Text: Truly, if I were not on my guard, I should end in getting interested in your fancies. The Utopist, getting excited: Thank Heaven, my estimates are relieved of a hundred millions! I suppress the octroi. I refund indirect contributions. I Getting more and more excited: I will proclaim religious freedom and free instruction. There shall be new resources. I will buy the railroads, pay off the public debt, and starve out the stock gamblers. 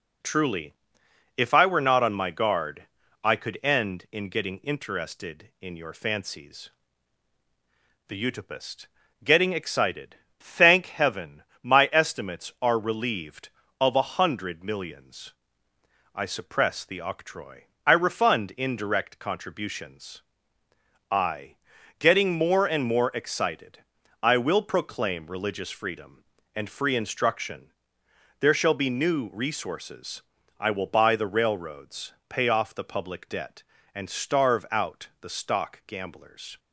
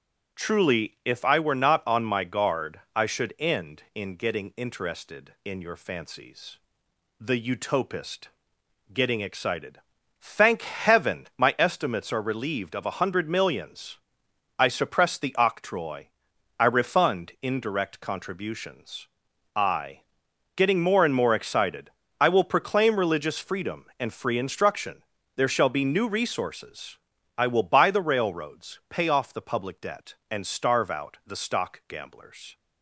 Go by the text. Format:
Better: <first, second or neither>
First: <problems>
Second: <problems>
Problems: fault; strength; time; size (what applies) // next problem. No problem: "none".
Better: second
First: says "could" for "should"; at 3.3 s // pauses between "I" and "Getting"; at 21.5 s; 0.44 s long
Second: pauses between "I" and "Getting"; noticeable; at 20.0 s; 0.54 s long